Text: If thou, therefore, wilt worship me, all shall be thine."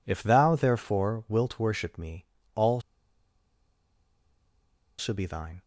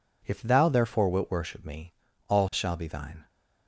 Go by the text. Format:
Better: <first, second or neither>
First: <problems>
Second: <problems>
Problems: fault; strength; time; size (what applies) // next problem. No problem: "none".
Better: second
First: pauses between "all" and "shall"; strong; at 2.8 s; 2.1 s long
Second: none